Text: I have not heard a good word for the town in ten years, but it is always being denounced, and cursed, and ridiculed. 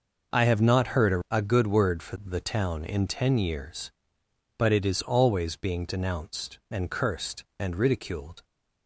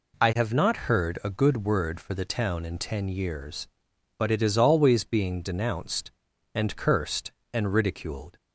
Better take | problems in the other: second | says "a" twice; at 1.2 s

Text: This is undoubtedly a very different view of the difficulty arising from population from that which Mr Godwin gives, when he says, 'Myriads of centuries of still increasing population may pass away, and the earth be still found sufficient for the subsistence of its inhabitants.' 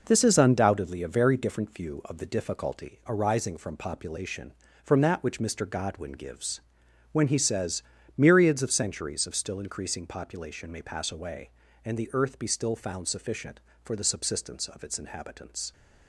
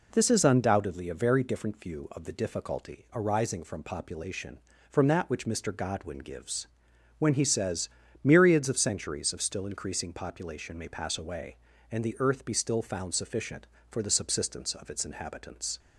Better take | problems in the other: second | gets quieter; strong; throughout; 7 dB

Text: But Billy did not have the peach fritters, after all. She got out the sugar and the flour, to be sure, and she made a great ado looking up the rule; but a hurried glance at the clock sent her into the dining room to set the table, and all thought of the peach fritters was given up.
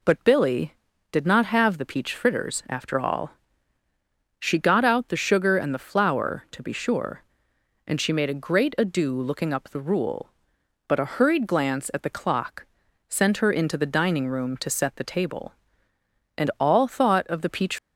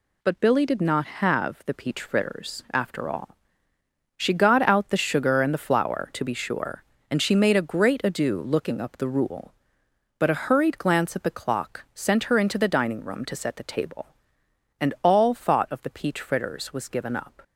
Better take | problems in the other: second | pauses between "clock" and "sent"; at 12.6 s; 0.44 s long // stops before "fritters was given up"; at 17.7 s

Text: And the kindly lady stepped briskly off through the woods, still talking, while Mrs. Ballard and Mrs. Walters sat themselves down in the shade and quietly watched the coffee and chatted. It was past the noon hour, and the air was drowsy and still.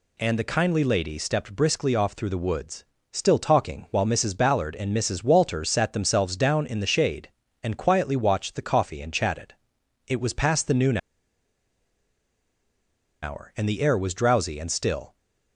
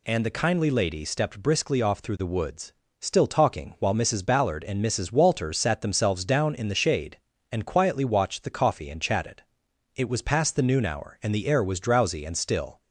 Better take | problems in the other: second | pauses between "noon" and "hour"; strong; at 10.9 s; 2.2 s long

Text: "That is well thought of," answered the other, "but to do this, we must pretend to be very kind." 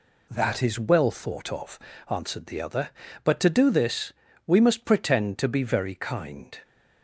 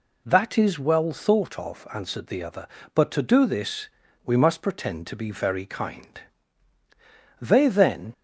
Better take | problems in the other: first | goes on to say "They then"; noticeable; from 7.4 s on; 0.72 s long

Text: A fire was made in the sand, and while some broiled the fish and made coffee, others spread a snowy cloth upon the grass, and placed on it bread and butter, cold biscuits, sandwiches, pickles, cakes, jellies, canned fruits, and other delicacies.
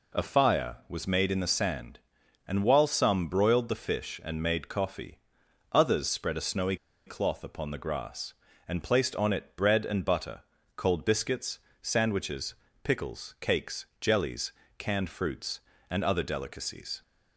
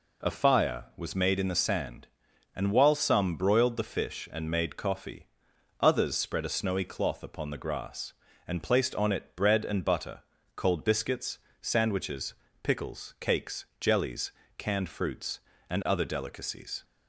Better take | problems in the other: second | pauses between "snowy" and "cloth"; slight; at 6.7 s; 0.31 s long

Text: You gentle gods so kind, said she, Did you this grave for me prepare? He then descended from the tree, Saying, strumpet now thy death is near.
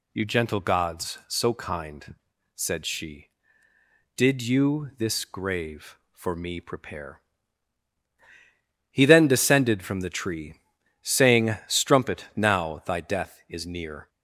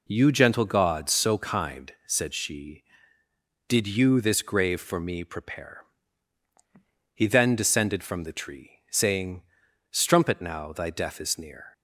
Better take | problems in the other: neither | none

